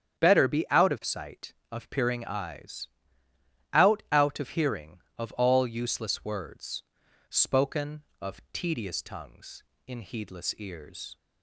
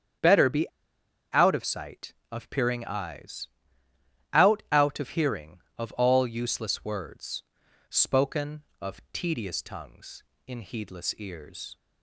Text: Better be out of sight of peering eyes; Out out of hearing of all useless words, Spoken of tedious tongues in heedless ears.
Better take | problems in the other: first | starts louder than the rest; strong; until 1.8 s; 8.5 dB; strong in the first // pauses between "be" and "out"; noticeable; at 0.6 s; 0.67 s long

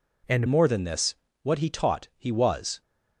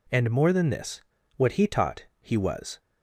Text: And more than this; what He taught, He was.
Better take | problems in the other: second | changes voice at "more"; from 0.4 s on; 2.4 s long

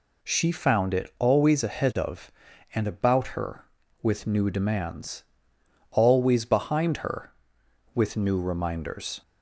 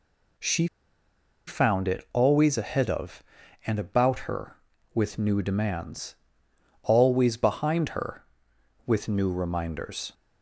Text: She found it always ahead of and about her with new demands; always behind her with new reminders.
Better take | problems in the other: first | pauses between "She" and "found"; noticeable; at 0.6 s; 0.80 s long

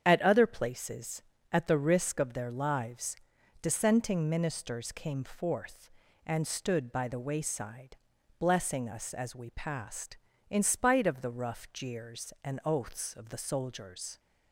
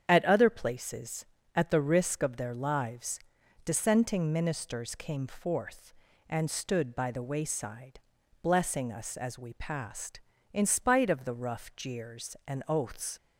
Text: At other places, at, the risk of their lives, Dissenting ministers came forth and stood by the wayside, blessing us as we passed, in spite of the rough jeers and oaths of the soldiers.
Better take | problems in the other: first | starts louder than the rest; strong; until 1.0 s; 8 dB; strong in the first // stops before "of the soldiers"; at 13.1 s

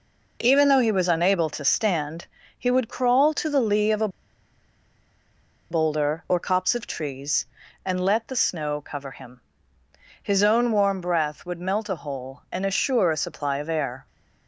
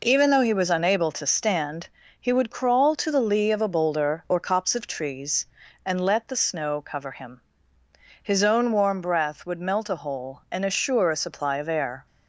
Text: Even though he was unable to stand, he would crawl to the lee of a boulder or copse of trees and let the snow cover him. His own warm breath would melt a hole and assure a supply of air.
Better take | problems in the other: second | pauses between "a" and "boulder"; strong; at 4.0 s; 1.6 s long

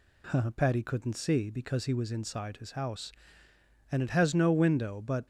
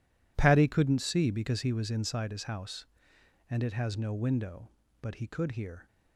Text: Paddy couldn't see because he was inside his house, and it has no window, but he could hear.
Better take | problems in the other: second | stops before "he could hear"; at 5.2 s

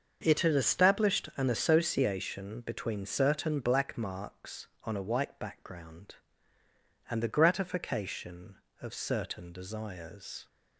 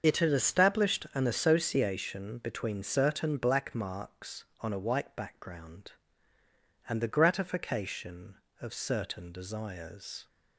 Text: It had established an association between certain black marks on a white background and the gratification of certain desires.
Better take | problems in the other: first | loses the start of "It"; at 0.0 s; 60 ms // starts louder than the rest; until 1.0 s; 6.5 dB; also in the first

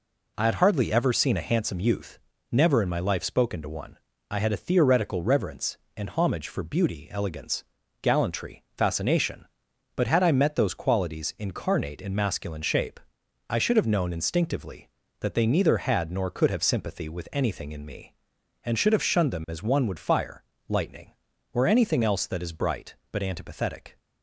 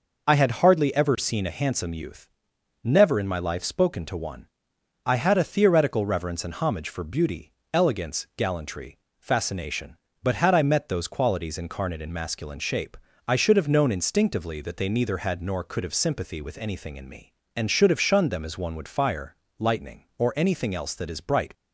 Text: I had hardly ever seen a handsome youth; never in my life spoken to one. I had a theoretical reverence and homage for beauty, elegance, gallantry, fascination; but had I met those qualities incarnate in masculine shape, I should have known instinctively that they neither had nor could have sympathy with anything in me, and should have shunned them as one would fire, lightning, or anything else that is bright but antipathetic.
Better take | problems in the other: first | stops before "but antipathetic"; at 21.5 s

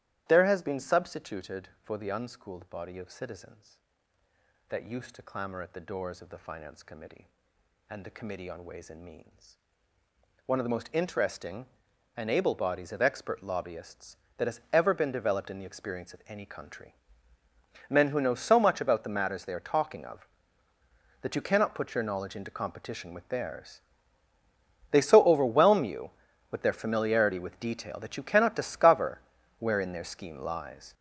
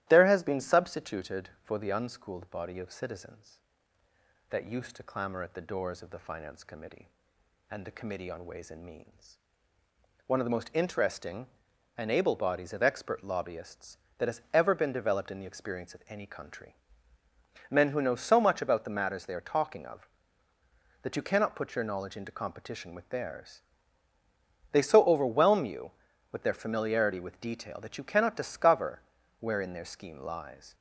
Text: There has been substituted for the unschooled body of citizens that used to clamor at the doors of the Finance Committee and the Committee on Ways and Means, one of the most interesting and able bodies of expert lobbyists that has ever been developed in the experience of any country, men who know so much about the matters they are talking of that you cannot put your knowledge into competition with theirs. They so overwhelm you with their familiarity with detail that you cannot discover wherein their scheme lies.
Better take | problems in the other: second | gets louder; strong; throughout; 9.5 dB // starts louder than the rest; strong; until 1.2 s; 13 dB; strong in the second // pauses between "discover" and "wherein"; at 29.2 s; 0.38 s long; also in the second

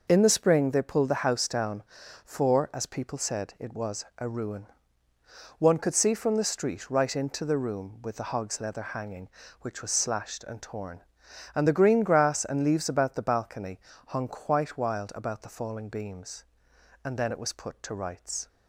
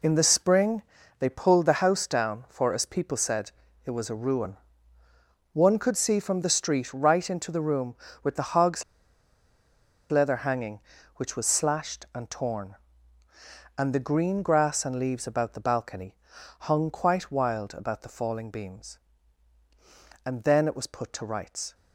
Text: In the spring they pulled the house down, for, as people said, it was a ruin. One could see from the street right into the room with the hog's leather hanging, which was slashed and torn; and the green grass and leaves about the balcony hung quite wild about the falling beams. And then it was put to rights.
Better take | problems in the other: first | pauses between "spring" and "they"; at 0.8 s; 0.38 s long // pauses between "hog's" and "leather"; strong; at 8.8 s; 1.2 s long // pauses between "balcony" and "hung"; noticeable; at 16.1 s; 0.46 s long; slight in the first

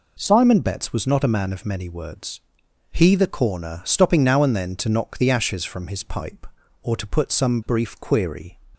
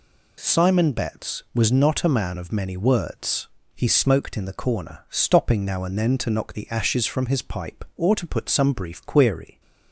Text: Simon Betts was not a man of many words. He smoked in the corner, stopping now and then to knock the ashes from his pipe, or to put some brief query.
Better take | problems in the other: second | skips "smoked in"; at 3.1 s

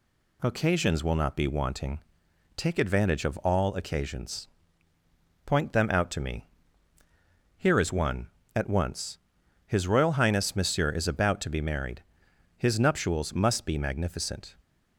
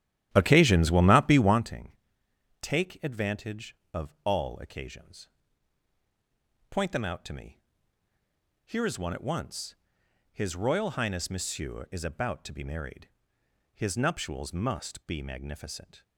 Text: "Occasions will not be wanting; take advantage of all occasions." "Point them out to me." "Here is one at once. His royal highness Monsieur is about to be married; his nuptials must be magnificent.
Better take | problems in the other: first | starts louder than the rest; strong; until 1.7 s; 12 dB

